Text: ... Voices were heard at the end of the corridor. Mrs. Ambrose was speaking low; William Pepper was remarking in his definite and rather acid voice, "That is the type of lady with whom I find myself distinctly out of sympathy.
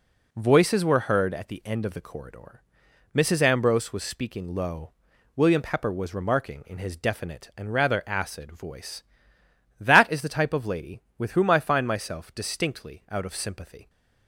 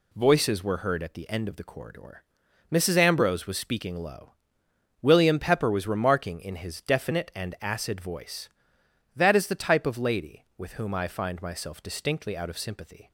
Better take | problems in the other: first | skips "rather"; at 7.5 s

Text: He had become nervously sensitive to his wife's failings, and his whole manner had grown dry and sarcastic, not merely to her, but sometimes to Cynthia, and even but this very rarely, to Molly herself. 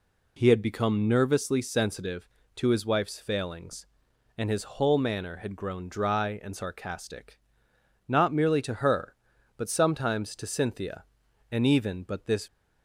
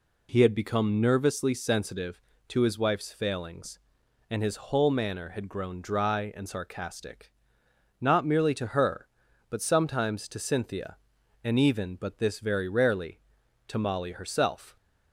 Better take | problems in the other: second | stops before "very rarely to Molly herself"; at 12.4 s

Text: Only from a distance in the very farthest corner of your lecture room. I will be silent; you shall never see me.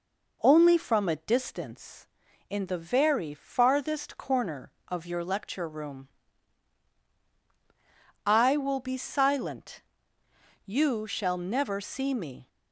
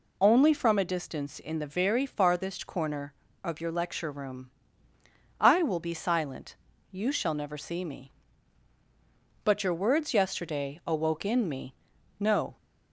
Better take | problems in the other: first | goes on to say "But your words yesterday awoke in me no"; strong; from 9.4 s on; 3.1 s long

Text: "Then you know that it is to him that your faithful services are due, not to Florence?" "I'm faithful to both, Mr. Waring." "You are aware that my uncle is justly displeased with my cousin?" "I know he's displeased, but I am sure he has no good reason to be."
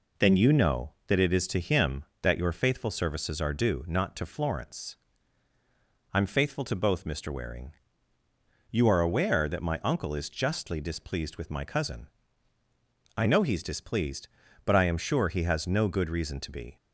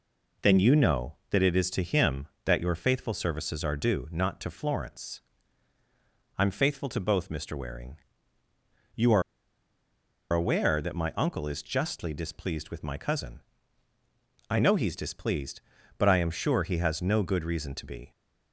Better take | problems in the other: first | pauses between "are" and "aware"; at 9.2 s; 1.1 s long

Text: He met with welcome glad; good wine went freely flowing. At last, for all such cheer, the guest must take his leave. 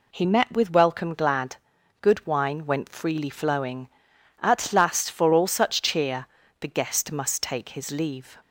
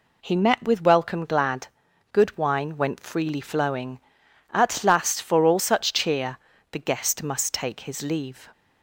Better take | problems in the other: neither | none

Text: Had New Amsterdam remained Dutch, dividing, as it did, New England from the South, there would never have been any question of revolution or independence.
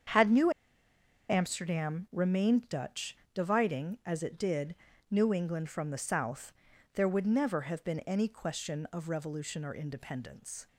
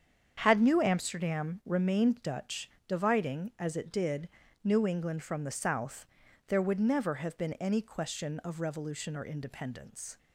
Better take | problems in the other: second | starts louder than the rest; strong; until 1.9 s; 7.5 dB; strong in the second // pauses between "New" and "Amsterdam"; noticeable; at 0.5 s; 0.79 s long

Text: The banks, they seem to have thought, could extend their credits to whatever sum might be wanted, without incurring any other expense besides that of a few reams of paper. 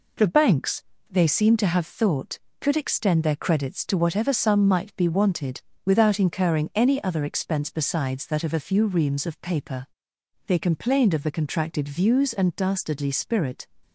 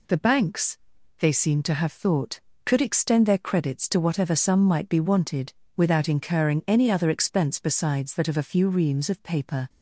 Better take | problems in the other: second | goes on to say "They complained of the contracted views and dastardly spirit"; strong; from 10.4 s on; 3.2 s long

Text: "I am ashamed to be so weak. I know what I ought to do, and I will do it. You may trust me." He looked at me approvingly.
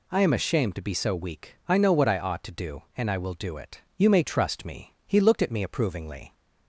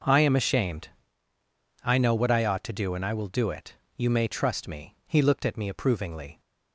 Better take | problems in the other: first | skips "to be so weak"; at 1.3 s

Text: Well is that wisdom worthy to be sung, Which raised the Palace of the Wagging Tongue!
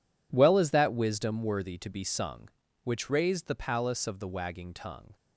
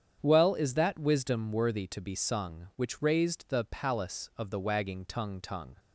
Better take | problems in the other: first | starts louder than the rest; strong; until 1.2 s; 8.5 dB // says "Tongue" twice; at 5.3 s

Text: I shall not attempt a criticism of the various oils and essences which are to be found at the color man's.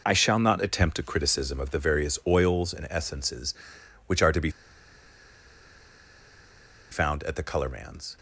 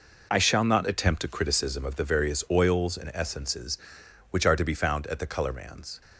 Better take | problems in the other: second | pauses between "be" and "found"; strong; at 4.4 s; 2.4 s long

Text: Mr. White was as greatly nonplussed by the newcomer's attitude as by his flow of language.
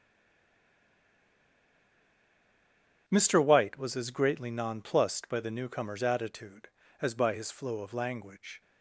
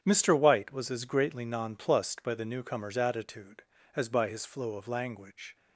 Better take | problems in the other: second | stays silent before the first word; strong; until 3.0 s; 3.0 s long // starts louder than the rest; strong; until 4.0 s; 8 dB; strong in the second

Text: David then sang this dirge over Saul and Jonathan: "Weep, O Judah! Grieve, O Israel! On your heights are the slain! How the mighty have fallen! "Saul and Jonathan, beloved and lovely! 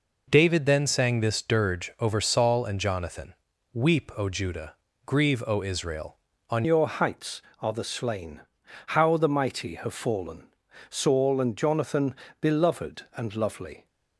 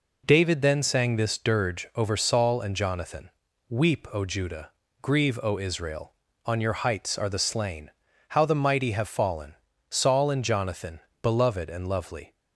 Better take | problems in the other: second | changes voice at "your"; from 6.6 s on; 7.2 s long

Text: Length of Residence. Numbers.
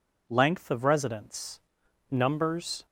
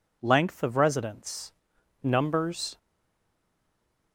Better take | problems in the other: first | stays silent after the last word; noticeable; from 2.7 s on; 1.4 s long

